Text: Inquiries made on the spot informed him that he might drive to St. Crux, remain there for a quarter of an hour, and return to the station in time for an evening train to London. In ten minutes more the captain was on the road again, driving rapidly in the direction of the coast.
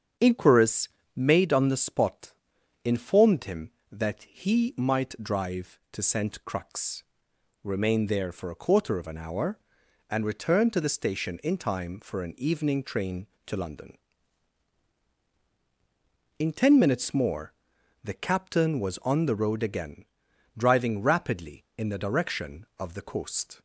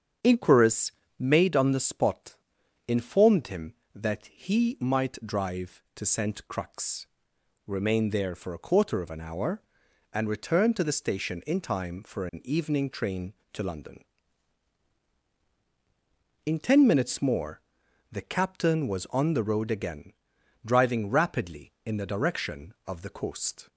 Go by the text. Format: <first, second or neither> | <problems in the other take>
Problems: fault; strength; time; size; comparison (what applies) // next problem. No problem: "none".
neither | starts louder than the rest; strong; the same in both // pauses between "Inquiries" and "made"; slight; the same in both // pauses between "spot" and "informed"; noticeable; the same in both // pauses between "more" and "the"; noticeable; the same in both